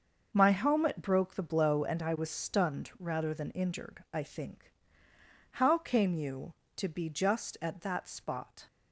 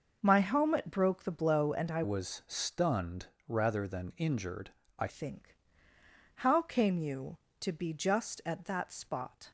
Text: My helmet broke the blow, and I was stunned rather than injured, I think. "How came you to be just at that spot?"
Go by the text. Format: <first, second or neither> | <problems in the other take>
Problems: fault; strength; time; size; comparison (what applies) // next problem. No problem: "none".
first | starts louder than the rest; noticeable; until 1.2 s; 6 dB; also in the first // changes voice from "was" to "I"; from 2.0 to 5.0 s; 3.0 s long // pauses between "stunned" and "rather"; slight; at 3.2 s; 0.20 s long